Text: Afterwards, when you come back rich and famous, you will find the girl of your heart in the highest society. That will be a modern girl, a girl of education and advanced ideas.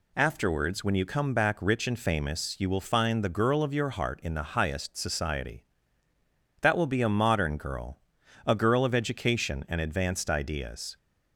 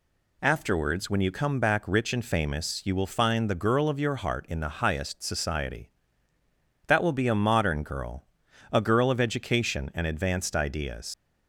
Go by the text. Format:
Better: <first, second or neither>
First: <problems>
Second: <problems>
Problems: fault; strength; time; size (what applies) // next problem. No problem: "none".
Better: first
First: none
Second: leaves "ideas" unfinished; at 11.1 s; 90 ms